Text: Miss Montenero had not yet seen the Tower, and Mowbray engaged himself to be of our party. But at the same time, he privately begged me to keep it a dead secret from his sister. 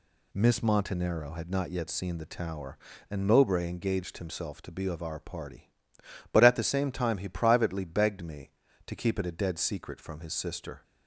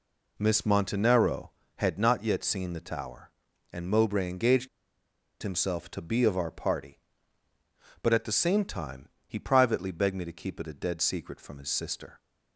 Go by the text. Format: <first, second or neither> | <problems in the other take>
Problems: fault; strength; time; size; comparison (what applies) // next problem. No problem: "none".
first | pauses between "engaged" and "himself"; noticeable; at 4.6 s; 0.72 s long